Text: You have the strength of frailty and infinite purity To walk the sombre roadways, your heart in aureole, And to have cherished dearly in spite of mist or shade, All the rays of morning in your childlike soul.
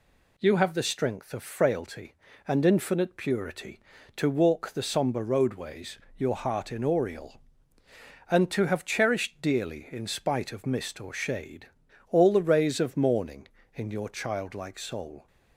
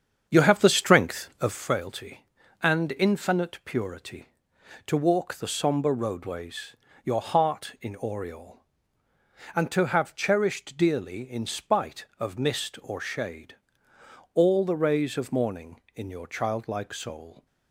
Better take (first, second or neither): first